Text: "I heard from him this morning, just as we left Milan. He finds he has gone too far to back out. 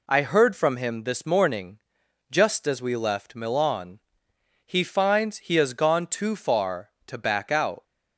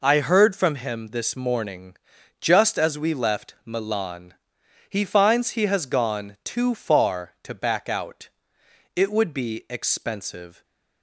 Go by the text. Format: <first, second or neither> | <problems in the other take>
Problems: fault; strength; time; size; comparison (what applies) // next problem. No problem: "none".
first | goes on to say "It would be expensive"; strong; from 8.9 s on; 1.6 s long // stays silent after the last word; slight; from 10.5 s on; 0.5 s long